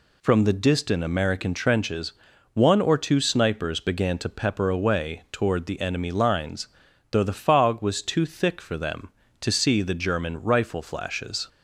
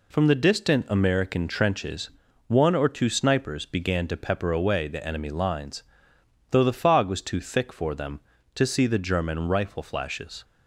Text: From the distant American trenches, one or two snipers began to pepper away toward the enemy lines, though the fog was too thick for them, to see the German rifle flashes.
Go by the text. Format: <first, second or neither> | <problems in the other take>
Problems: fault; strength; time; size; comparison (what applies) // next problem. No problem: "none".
first | skips "toward"; at 4.8 s